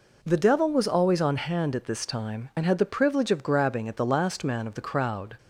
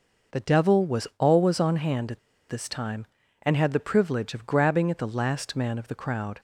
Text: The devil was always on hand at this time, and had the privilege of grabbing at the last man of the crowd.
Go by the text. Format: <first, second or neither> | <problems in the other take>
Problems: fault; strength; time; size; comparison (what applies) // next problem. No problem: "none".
first | pauses between "at" and "this"; slight; at 2.1 s; 0.29 s long